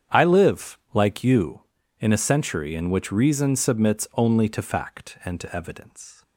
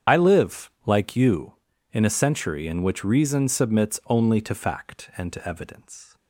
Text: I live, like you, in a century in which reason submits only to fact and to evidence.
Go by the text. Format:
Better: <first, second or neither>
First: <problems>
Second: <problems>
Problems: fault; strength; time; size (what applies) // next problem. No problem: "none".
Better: first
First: starts louder than the rest; strong; until 1.2 s; 8.5 dB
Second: loses the start of "I"; at 0.0 s; 45 ms // starts louder than the rest; strong; until 1.2 s; 8 dB